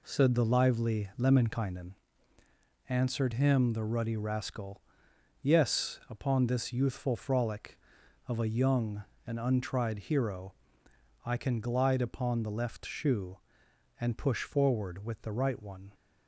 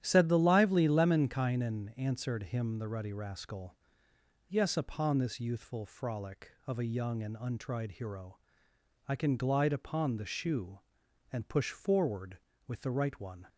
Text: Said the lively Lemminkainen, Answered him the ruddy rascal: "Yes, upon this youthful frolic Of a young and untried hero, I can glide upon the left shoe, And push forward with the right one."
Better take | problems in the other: first | starts louder than the rest; strong; until 1.0 s; 10.5 dB // skips "left"; at 10.2 s

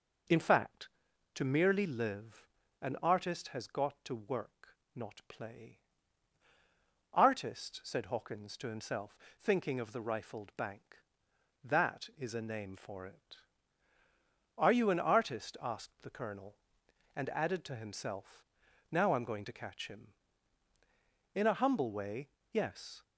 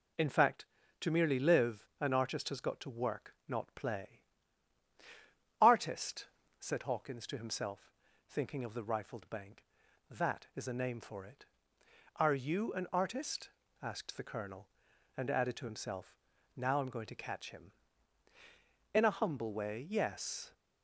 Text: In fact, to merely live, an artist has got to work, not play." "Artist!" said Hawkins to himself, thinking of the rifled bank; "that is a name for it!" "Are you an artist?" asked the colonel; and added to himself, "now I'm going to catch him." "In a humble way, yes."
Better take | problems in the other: neither | none

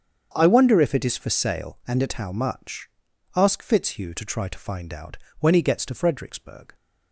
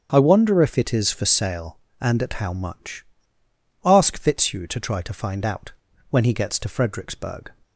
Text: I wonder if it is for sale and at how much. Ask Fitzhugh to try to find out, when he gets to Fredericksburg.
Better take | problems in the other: neither | starts louder than the rest; strong; the same in both

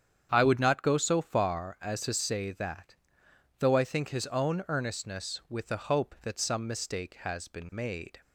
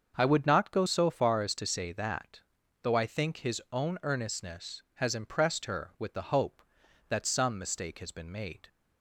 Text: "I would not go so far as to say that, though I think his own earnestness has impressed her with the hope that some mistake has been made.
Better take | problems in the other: second | starts louder than the rest; strong; until 1.3 s; 8 dB; also in the second // skips "has impressed her"; at 5.4 s

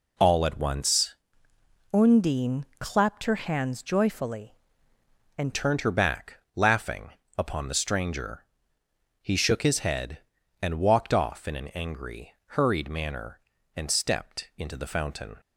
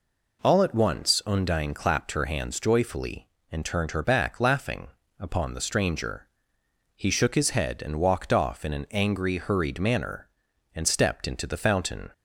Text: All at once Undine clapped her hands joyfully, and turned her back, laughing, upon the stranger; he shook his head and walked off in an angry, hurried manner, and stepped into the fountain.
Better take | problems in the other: second | changes voice from "Undine" to "and"; from 1.9 to 5.5 s; 3.6 s long

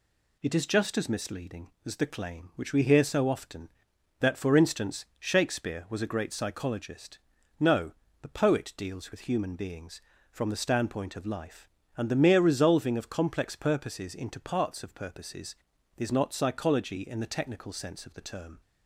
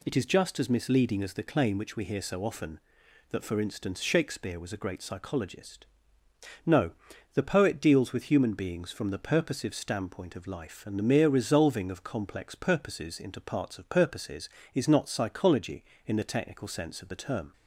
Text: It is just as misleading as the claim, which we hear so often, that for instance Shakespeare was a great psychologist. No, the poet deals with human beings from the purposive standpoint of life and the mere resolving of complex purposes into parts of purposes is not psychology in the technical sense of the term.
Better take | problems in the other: second | skips "purposive"; at 10.5 s

